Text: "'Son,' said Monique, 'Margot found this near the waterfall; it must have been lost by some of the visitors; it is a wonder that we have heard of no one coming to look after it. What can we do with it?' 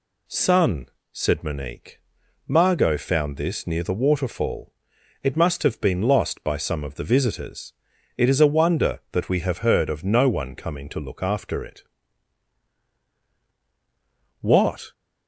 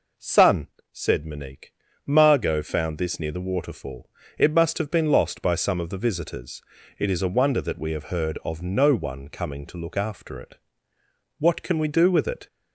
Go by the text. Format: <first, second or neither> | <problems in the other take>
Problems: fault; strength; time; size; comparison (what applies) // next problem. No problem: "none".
second | stops before "can we do with it"; at 14.9 s